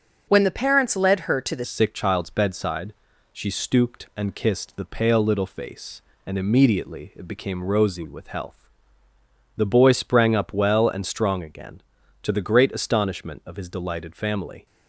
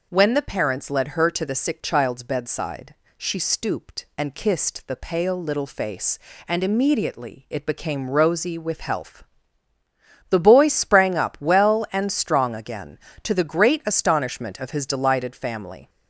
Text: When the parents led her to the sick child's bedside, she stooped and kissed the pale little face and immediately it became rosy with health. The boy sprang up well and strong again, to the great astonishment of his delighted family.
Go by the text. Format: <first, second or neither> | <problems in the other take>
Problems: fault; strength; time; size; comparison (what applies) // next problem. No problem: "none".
second | starts louder than the rest; until 1.2 s; 6.5 dB // changes voice at "sick"; from 1.6 s on; 13.0 s long